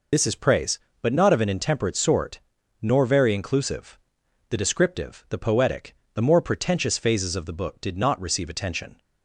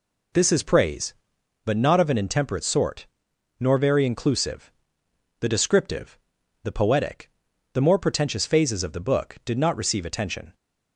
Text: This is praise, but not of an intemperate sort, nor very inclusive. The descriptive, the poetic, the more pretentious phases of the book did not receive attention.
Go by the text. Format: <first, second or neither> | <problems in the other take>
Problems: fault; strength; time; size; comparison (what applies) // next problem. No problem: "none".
second | loses the start of "This"; at 0.1 s; 40 ms